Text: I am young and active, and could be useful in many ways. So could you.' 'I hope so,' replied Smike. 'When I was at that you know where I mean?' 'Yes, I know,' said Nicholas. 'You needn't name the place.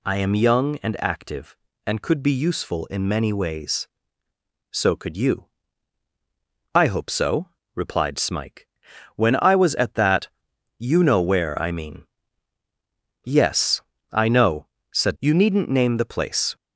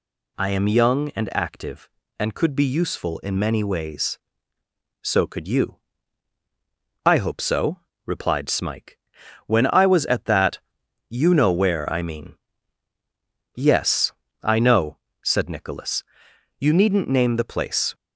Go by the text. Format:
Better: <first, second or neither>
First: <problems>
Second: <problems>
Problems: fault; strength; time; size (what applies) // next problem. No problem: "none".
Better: second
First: pauses between "that" and "you"; noticeable; at 10.2 s; 0.52 s long // skips "Nicholas"; at 15.1 s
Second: pauses between "that" and "you"; noticeable; at 10.5 s; 0.52 s long